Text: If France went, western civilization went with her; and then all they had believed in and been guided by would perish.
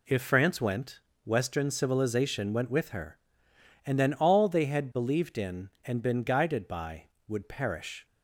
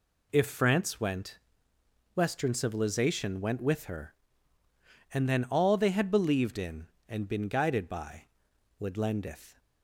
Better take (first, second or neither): first